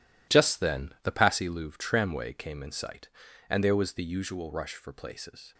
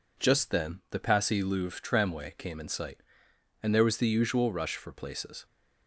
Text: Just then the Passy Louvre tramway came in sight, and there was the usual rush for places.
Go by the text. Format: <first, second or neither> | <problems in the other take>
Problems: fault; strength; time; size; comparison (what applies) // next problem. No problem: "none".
second | gets quieter; strong; throughout; 11.5 dB